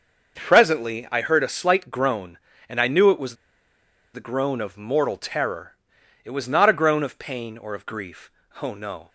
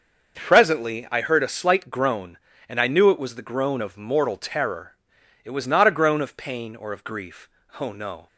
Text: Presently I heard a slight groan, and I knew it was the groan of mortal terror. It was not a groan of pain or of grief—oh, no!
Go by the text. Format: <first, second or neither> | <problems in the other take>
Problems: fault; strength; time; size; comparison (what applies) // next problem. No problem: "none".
second | starts louder than the rest; noticeable; until 1.3 s; 6 dB; noticeable in the second // pauses between "was" and "the"; noticeable; at 3.3 s; 0.79 s long